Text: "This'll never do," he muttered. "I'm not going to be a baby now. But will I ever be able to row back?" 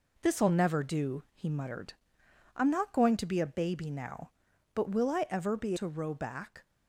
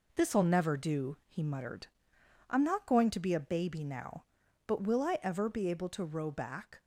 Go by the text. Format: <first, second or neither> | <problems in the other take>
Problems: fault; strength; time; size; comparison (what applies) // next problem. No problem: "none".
second | skips "able"; at 5.7 s